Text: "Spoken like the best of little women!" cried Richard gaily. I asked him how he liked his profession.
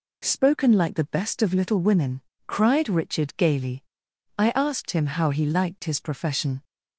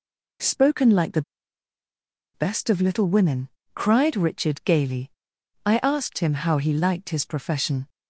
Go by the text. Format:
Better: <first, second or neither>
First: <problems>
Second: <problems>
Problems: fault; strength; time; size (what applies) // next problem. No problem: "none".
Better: first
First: none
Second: pauses between "the" and "best"; at 1.2 s; 1.1 s long